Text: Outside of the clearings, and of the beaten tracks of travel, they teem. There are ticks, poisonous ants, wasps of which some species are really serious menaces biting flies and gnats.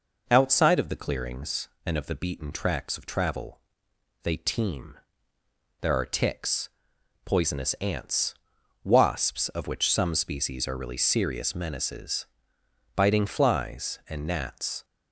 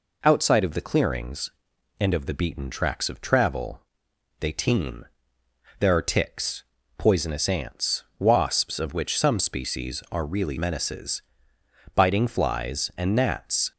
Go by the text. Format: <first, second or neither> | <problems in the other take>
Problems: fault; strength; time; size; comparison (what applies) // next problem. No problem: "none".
first | skips "serious"; at 10.5 s // pauses between "menaces" and "biting"; noticeable; at 11.2 s; 0.74 s long; noticeable in the first